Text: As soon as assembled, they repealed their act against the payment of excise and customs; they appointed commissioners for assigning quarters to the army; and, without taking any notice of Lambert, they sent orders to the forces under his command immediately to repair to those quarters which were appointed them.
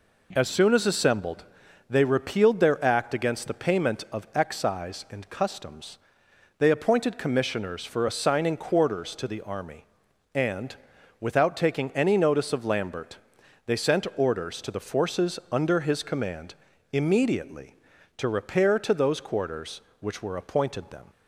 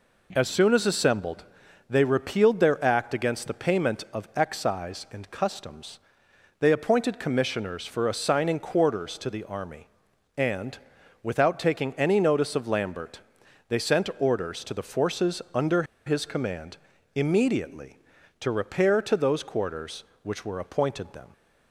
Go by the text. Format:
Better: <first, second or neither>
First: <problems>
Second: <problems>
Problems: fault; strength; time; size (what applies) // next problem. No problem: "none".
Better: first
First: pauses between "command" and "immediately"; at 16.5 s; 0.40 s long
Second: pauses between "under" and "his"; slight; at 15.8 s; 0.22 s long // pauses between "command" and "immediately"; at 16.7 s; 0.40 s long